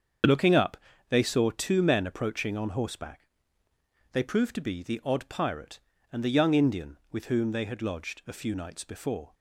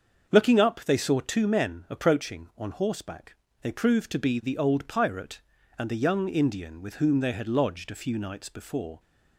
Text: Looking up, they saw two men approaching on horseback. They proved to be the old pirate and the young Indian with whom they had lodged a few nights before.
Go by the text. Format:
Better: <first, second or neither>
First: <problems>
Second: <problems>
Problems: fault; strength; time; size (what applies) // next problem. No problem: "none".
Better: second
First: starts louder than the rest; until 1.5 s; 7 dB // says "odd" for "old"; at 5.0 s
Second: starts louder than the rest; until 1.3 s; 7 dB